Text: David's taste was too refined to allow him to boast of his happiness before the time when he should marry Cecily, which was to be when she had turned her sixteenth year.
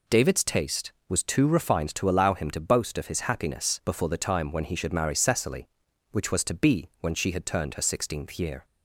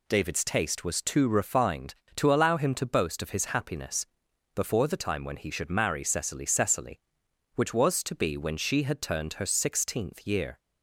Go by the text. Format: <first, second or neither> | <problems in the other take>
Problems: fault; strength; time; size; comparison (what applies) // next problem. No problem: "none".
first | pauses between "happiness" and "before"; noticeable; at 4.0 s; 0.48 s long // says "Cecily" twice; at 6.4 s